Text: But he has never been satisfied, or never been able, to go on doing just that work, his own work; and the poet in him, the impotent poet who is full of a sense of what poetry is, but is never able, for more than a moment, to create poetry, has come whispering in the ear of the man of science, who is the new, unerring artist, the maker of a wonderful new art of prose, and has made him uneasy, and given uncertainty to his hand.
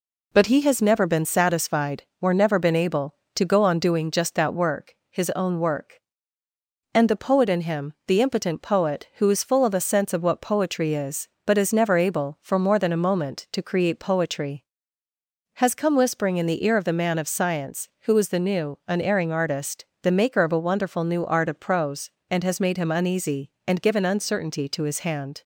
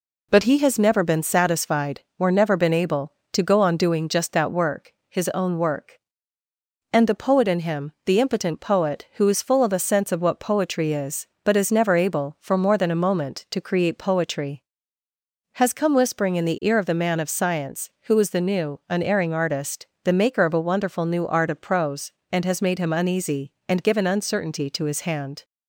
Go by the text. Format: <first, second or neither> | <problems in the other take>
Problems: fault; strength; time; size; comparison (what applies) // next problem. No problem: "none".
neither | none